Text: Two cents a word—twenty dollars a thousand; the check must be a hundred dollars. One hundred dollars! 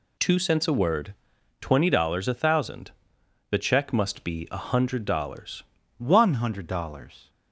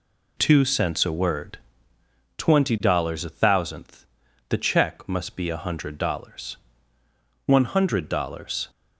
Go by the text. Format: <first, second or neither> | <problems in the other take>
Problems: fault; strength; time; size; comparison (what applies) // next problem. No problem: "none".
first | says "thousandth" for "thousand"; at 3.2 s